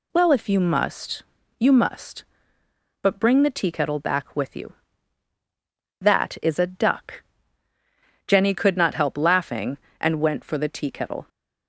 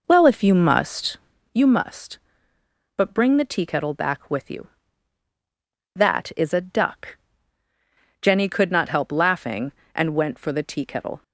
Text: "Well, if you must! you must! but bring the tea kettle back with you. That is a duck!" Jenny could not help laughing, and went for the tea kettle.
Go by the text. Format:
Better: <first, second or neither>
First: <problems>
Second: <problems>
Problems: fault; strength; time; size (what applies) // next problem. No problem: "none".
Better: first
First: none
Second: starts louder than the rest; noticeable; until 1.6 s; 5 dB